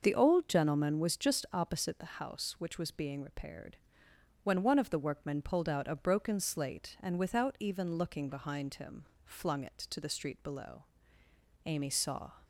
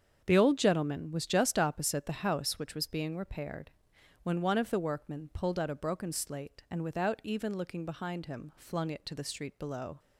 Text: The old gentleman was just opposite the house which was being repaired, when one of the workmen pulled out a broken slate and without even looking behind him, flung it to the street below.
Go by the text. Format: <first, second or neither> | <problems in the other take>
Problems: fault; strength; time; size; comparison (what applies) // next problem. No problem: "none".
second | starts louder than the rest; noticeable; until 1.0 s; 6 dB; strong in the second // goes on to say "Amy saw"; noticeable; from 11.6 s on; 0.68 s long